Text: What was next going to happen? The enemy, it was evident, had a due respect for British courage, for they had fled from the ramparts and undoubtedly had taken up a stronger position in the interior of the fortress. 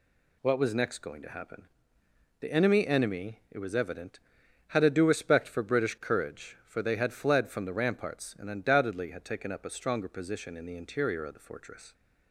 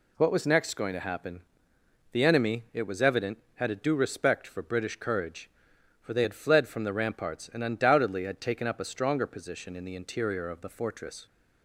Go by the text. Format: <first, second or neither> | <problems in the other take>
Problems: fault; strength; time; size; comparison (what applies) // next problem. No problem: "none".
second | says "enemy" twice; at 2.8 s